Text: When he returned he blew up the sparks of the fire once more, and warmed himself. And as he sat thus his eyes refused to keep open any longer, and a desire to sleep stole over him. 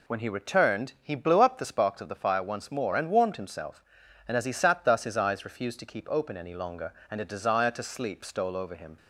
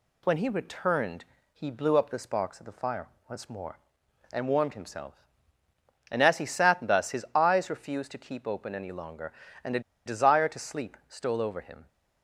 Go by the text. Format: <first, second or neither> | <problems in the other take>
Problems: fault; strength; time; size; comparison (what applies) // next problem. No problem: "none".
first | pauses between "returned" and "he"; slight; at 1.2 s; 0.26 s long // pauses between "fire" and "once"; slight; at 3.0 s; 0.20 s long // pauses between "a" and "desire"; slight; at 9.8 s; 0.25 s long